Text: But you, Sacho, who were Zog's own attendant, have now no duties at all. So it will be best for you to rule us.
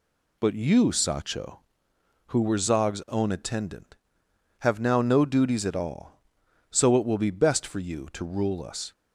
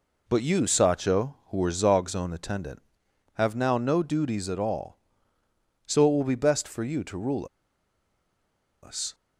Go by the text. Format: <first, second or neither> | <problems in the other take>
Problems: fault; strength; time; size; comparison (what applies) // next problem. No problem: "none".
first | pauses between "rule" and "us"; strong; at 7.4 s; 1.3 s long